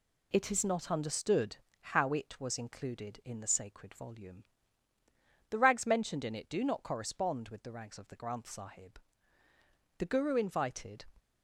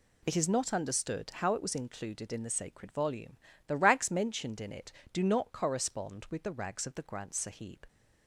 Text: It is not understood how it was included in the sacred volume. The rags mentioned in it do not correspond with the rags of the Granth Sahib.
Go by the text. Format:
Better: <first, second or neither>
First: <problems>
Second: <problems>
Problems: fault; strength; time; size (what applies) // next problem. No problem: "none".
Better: second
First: pauses between "understood" and "how"; slight; at 1.5 s; 0.22 s long // goes on to say "The Guru invited"; noticeable; from 9.9 s on; 1.0 s long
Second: none